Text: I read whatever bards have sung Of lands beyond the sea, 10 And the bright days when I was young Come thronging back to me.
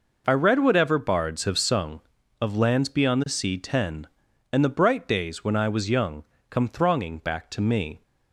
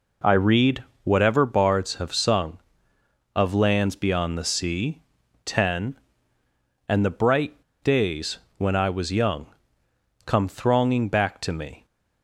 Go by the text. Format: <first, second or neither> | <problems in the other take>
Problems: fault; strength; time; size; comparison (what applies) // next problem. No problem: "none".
first | pauses between "read" and "whatever"; slight; at 0.8 s; 0.18 s long // pauses between "bright" and "days"; slight; at 7.6 s; 0.19 s long // pauses between "days" and "when"; slight; at 8.3 s; 0.18 s long // pauses between "young" and "Come"; noticeable; at 9.4 s; 0.78 s long; slight in the first